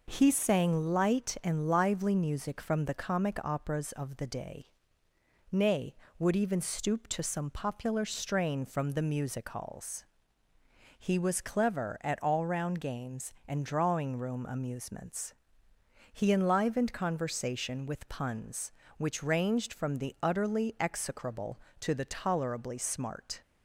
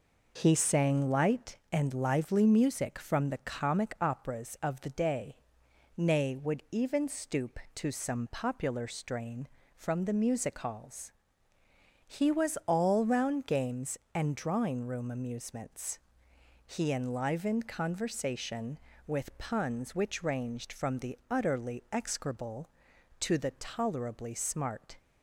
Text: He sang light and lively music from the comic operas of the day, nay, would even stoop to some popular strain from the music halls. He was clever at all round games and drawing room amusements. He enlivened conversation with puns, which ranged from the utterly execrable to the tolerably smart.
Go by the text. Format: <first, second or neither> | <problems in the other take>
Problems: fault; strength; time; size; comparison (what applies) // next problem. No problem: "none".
first | skips "clever at"; at 12.6 s